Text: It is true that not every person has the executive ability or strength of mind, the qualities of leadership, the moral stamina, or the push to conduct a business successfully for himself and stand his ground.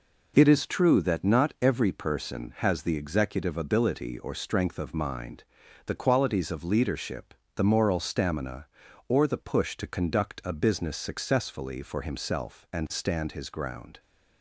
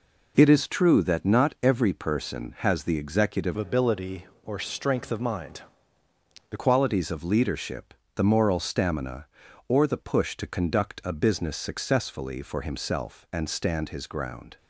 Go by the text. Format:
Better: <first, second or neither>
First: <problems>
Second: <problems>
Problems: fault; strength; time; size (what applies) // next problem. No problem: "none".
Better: first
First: none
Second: changes voice from "ability" to "the"; from 3.5 to 6.5 s; 3.0 s long